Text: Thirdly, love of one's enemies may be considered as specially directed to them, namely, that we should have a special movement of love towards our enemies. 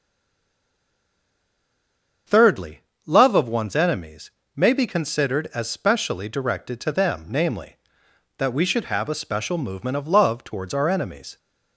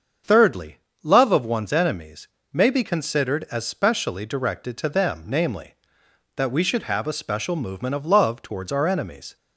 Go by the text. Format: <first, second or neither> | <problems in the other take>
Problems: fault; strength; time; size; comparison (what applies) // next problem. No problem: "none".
second | stays silent before the first word; until 2.2 s; 2.2 s long // starts louder than the rest; until 3.5 s; 7 dB; also in the second // pauses between "enemies" and "may"; slight; at 4.3 s; 0.22 s long; slight in the second